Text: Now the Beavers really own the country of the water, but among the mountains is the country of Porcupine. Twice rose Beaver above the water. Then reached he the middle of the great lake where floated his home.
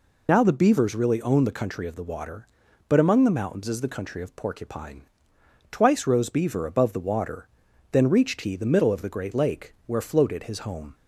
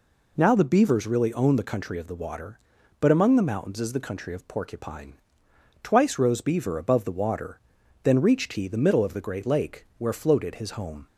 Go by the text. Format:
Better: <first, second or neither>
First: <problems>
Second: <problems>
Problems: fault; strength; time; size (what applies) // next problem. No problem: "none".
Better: second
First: loses the start of "Now"; at 0.2 s; 45 ms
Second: none